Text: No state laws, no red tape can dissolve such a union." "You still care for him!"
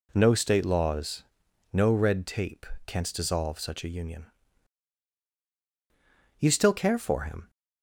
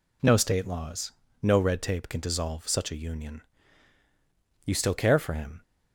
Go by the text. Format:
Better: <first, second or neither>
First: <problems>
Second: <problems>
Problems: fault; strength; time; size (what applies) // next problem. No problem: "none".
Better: second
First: says "canst" for "can"; at 2.8 s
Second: none